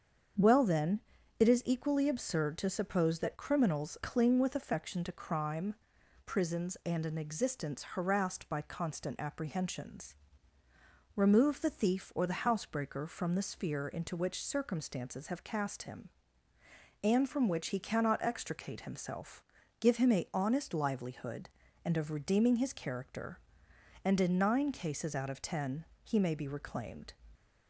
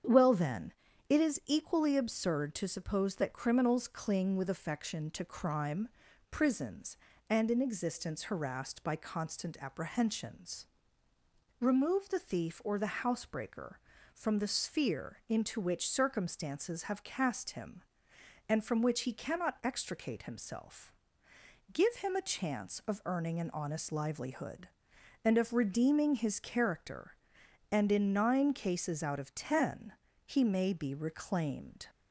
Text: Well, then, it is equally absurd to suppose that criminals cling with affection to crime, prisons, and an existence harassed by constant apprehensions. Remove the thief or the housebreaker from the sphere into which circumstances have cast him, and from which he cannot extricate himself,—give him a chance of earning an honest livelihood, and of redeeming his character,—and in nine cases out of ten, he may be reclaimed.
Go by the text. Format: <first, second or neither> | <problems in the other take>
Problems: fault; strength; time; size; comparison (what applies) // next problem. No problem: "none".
second | starts louder than the rest; strong; until 1.7 s; 7.5 dB; strong in the second // skips "chance of earning an"; at 20.3 s